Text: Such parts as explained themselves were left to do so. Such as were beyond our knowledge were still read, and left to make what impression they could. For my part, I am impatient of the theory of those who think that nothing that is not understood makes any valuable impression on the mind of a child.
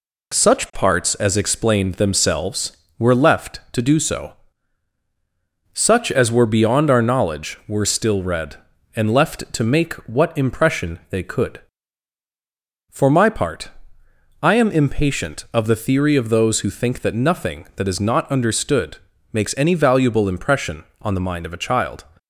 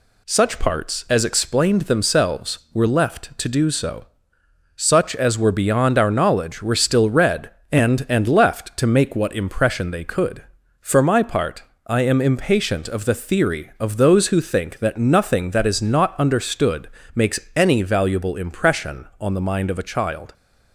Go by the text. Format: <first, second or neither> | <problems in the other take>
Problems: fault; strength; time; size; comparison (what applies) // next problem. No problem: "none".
first | says "and" twice; at 8.0 s // pauses between "understood" and "makes"; slight; at 16.8 s; 0.28 s long; slight in the first // pauses between "makes" and "any"; slight; at 17.3 s; 0.16 s long